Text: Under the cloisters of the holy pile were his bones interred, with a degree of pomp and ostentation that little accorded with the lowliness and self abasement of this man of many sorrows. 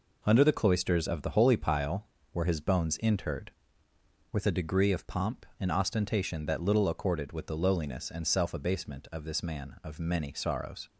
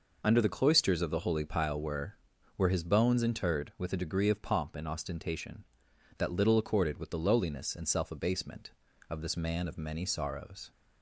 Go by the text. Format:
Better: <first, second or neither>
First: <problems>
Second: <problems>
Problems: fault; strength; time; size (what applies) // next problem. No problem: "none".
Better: first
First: none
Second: says "were" twice; at 2.5 s